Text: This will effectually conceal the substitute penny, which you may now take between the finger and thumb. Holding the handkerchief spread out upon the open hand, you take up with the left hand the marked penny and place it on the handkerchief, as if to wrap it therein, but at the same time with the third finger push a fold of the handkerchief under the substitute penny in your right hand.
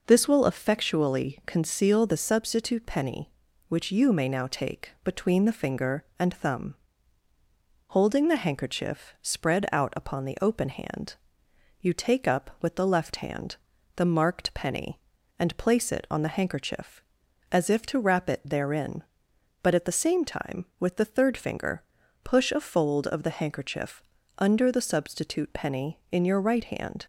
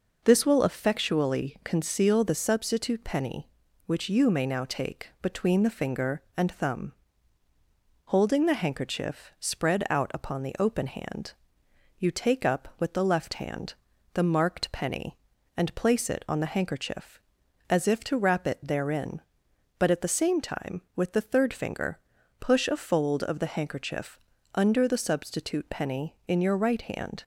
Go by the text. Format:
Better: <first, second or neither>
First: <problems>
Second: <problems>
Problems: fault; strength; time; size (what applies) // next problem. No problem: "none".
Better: neither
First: pauses between "hand" and "the"; at 13.5 s; 0.38 s long // pauses between "finger" and "push"; at 21.8 s; 0.42 s long // pauses between "handkerchief" and "under"; slight; at 24.0 s; 0.36 s long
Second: pauses between "hand" and "the"; at 13.7 s; 0.38 s long // pauses between "finger" and "push"; at 21.9 s; 0.42 s long // pauses between "handkerchief" and "under"; slight; at 24.1 s; 0.36 s long